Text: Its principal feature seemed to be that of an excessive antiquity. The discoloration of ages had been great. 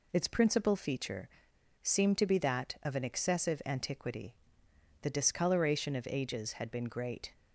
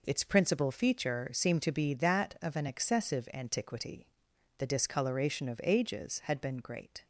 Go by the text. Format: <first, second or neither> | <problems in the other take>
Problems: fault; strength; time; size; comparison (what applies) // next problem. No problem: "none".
second | pauses between "feature" and "seemed"; noticeable; at 1.2 s; 0.55 s long